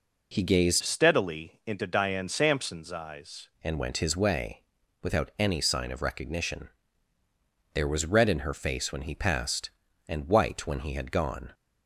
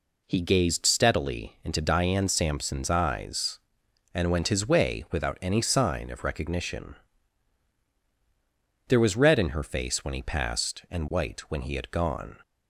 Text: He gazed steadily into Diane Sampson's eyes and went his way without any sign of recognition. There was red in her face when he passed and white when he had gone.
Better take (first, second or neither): second